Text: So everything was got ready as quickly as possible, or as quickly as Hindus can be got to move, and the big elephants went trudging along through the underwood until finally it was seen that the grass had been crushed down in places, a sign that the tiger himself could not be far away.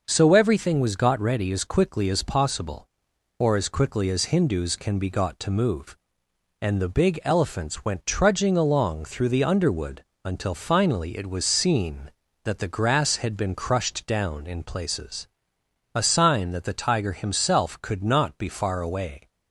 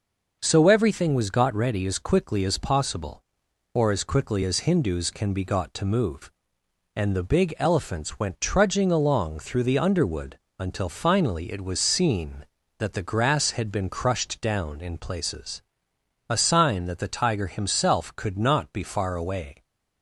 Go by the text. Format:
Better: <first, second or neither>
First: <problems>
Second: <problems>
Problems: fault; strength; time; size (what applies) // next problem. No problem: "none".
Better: neither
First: pauses between "underwood" and "until"; slight; at 10.0 s; 0.22 s long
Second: pauses between "underwood" and "until"; slight; at 10.3 s; 0.22 s long